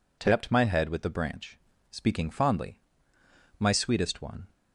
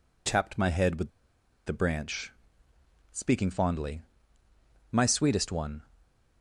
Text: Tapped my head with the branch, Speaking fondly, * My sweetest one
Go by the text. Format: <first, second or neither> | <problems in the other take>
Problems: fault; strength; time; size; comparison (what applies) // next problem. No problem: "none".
first | pauses between "with" and "the"; noticeable; at 1.0 s; 0.57 s long